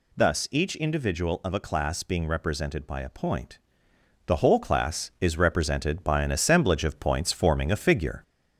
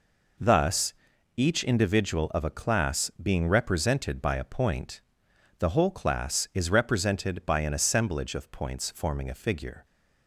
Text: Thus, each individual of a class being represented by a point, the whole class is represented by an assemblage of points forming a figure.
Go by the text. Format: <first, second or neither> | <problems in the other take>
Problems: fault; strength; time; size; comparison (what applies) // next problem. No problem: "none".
second | gets louder; slight; throughout; 2.5 dB